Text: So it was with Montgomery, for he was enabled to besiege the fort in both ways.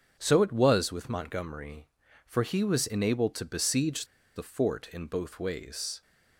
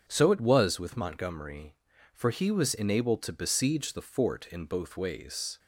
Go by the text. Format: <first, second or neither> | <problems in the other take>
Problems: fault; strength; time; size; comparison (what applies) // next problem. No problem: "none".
second | starts louder than the rest; until 1.1 s; 7 dB; strong in the second // pauses between "besiege" and "the"; slight; at 4.0 s; 0.29 s long